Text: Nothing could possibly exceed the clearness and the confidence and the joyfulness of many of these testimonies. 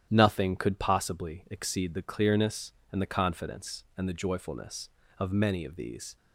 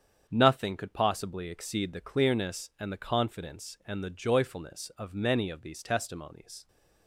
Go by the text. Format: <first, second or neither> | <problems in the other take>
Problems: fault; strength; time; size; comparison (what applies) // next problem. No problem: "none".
second | starts louder than the rest; strong; until 1.1 s; 10.5 dB; strong in the second // stops before "testimonies"; at 6.1 s